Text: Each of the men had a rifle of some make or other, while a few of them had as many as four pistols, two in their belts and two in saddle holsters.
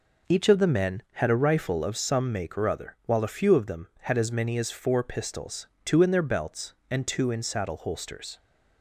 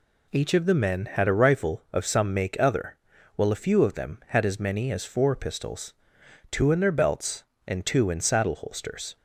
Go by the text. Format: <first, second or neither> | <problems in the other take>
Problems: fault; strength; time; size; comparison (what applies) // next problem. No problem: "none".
first | skips "or"; at 2.5 s